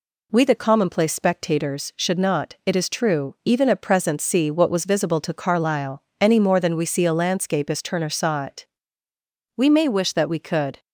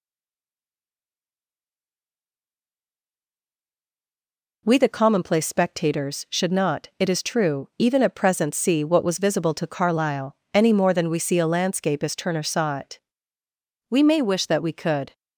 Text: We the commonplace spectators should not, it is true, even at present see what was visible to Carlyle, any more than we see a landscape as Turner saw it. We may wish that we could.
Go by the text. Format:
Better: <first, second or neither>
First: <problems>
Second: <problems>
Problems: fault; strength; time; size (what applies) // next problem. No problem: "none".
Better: first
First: none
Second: stays silent before the first word; strong; until 4.6 s; 4.6 s long